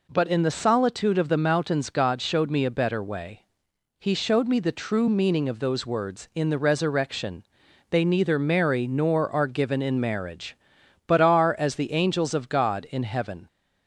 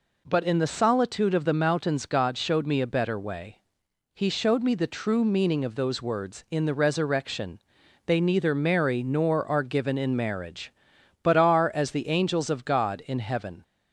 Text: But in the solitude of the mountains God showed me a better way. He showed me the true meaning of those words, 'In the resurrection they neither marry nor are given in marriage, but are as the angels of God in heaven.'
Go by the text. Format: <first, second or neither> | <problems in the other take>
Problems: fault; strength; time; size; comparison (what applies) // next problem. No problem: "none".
neither | pauses between "resurrection" and "they"; noticeable; the same in both